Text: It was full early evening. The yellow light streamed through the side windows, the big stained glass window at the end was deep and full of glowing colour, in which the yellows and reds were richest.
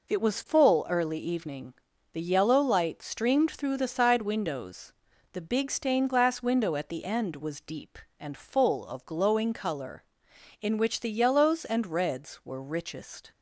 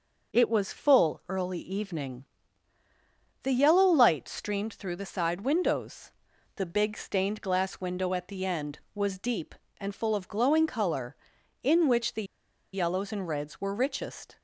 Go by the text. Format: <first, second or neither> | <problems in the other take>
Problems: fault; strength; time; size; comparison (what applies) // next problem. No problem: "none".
first | pauses between "the" and "yellows"; noticeable; at 12.2 s; 0.49 s long